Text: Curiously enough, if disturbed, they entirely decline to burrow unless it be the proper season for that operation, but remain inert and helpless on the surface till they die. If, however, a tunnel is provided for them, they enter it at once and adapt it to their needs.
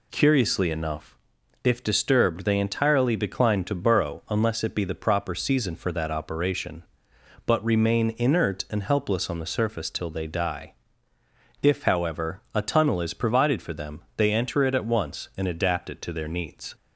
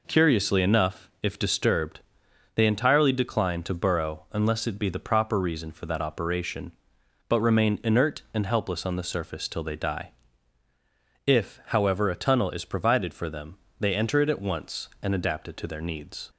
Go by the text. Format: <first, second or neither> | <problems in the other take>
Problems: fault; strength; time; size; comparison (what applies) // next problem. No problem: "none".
first | says "reason" for "season"; at 5.3 s